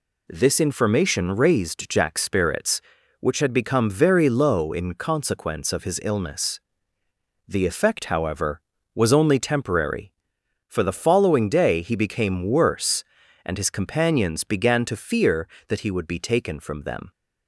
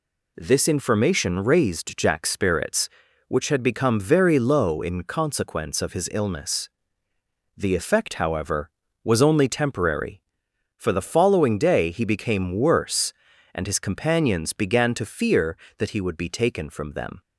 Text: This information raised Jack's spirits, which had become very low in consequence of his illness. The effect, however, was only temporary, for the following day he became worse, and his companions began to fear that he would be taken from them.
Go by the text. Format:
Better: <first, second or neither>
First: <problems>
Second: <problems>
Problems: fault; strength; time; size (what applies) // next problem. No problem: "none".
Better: neither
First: none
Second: none